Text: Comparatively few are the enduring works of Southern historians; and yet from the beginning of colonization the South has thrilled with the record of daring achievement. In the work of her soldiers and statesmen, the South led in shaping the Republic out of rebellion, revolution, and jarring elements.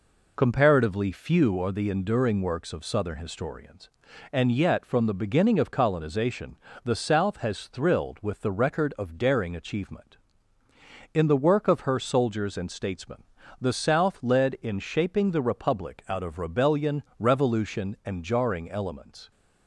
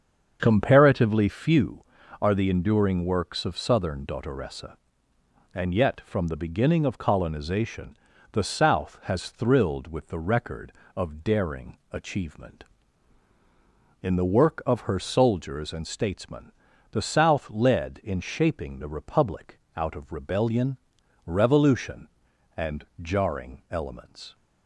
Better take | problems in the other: first | starts louder than the rest; strong; until 1.4 s; 7 dB // says "dottoressa" for "historians"; at 4.0 s // pauses between "colonization" and "the"; slight; at 7.9 s; 0.36 s long; slight in the first // pauses between "Republic" and "out"; slight; at 19.5 s; 0.18 s long

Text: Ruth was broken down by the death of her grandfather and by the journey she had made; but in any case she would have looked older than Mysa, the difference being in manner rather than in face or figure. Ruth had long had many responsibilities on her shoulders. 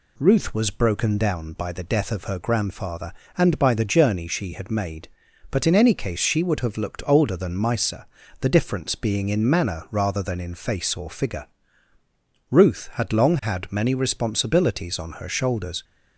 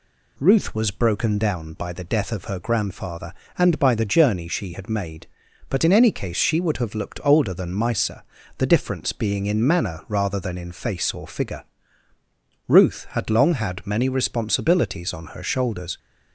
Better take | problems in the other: neither | none

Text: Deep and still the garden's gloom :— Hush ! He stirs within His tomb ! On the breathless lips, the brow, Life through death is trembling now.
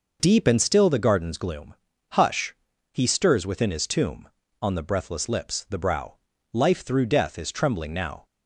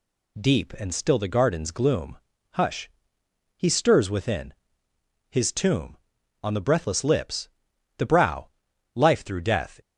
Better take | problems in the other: first | pauses between "within" and "His"; noticeable; at 4.5 s; 0.76 s long // stops before "is trembling now"; at 9.8 s

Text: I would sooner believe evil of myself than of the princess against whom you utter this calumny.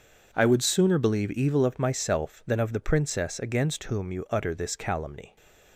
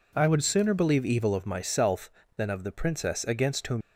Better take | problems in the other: first | stops before "you utter this calumny"; at 3.8 s

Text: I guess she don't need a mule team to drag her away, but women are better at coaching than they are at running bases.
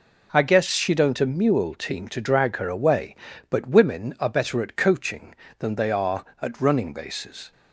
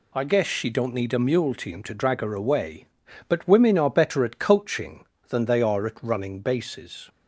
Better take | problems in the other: second | skips "need"; at 1.2 s

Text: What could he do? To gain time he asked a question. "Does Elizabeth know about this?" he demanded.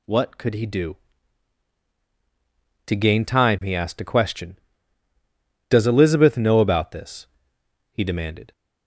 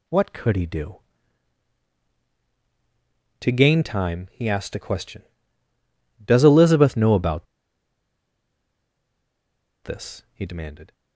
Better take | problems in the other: first | pauses between "about" and "this"; strong; at 7.4 s; 2.3 s long

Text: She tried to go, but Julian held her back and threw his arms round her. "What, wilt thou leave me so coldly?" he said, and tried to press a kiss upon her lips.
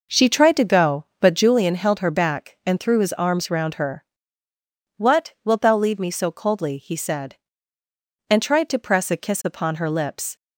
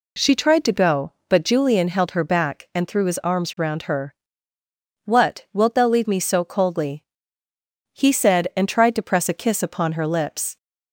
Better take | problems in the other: second | starts louder than the rest; noticeable; until 1.5 s; 6 dB

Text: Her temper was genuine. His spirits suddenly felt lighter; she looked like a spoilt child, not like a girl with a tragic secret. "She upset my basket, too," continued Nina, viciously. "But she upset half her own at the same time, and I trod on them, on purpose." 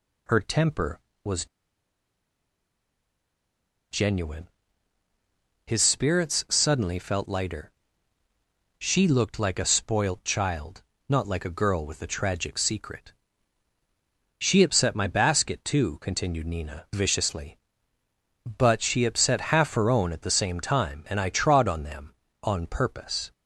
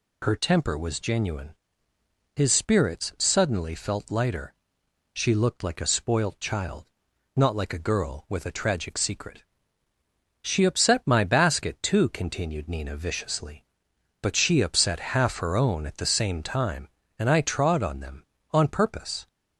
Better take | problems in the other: second | pauses between "was" and "genuine"; strong; at 1.4 s; 2.4 s long

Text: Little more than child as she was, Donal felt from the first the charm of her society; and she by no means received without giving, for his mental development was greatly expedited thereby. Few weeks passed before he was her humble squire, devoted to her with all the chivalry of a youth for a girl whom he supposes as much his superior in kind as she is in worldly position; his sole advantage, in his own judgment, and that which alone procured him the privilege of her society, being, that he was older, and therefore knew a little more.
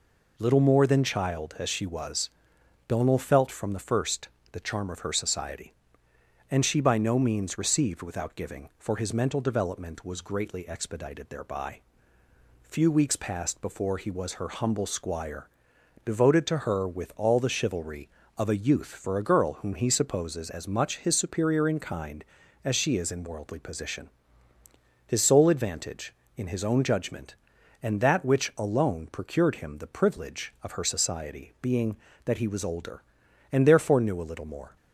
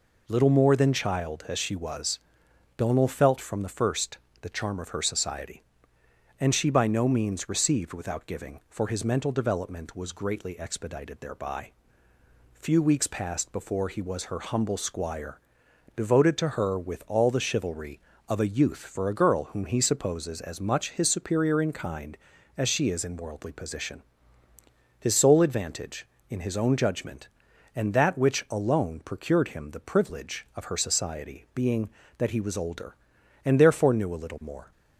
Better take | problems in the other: neither | pauses between "first" and "the"; slight; the same in both

